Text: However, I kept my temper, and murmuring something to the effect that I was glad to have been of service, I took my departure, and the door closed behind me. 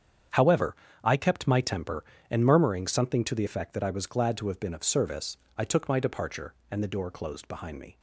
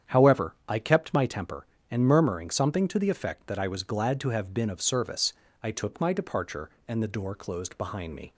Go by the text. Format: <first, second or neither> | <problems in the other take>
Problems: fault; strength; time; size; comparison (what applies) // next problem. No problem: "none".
neither | starts louder than the rest; strong; the same in both